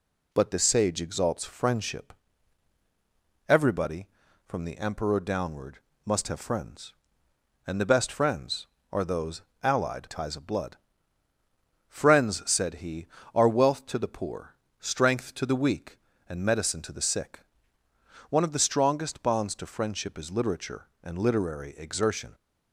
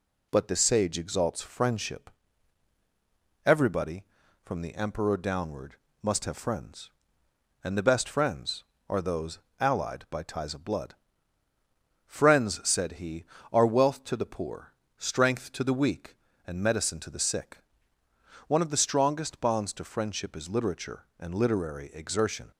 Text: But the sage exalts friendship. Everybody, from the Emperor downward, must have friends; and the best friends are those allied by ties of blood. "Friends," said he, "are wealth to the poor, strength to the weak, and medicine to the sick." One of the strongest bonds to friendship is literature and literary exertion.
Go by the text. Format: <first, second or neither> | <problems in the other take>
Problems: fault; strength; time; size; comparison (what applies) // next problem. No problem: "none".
second | pauses between "those" and "allied"; slight; at 9.4 s; 0.22 s long; slight in the second // skips "by"; at 10.0 s